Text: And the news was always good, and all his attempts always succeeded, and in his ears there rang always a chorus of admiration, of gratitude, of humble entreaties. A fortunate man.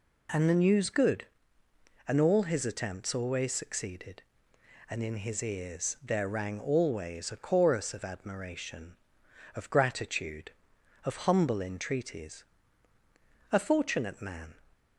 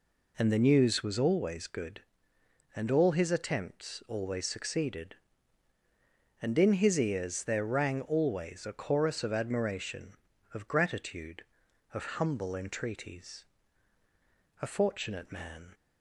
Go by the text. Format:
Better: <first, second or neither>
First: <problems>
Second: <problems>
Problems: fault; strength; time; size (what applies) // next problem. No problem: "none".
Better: second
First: skips "was always"; at 0.9 s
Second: none